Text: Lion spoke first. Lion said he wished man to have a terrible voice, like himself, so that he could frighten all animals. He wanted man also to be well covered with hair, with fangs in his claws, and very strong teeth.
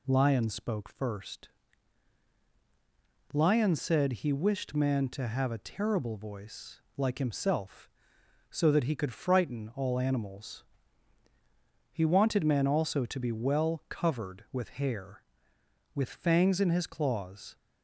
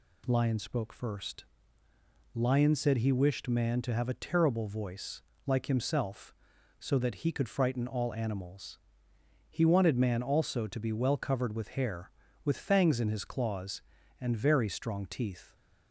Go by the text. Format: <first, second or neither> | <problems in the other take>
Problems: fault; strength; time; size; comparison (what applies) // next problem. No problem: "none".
second | stops before "and very strong teeth"; at 17.5 s